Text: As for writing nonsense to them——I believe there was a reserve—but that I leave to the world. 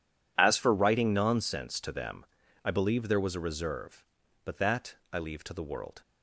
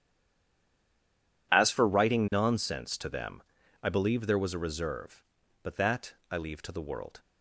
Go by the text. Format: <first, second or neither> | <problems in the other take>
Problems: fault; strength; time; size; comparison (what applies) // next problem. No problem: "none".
first | stays silent before the first word; noticeable; until 1.5 s; 1.5 s long // pauses between "that" and "I"; slight; at 6.1 s; 0.18 s long; slight in the first